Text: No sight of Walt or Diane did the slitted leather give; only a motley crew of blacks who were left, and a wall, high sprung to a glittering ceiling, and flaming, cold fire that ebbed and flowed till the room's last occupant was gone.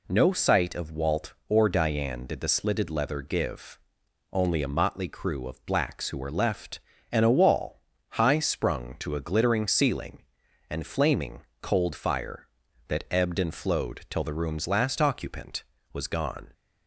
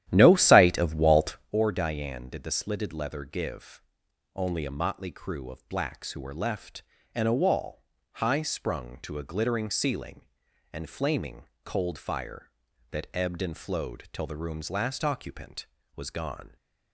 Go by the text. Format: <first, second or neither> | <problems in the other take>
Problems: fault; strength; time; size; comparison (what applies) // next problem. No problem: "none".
first | starts louder than the rest; strong; until 1.6 s; 12 dB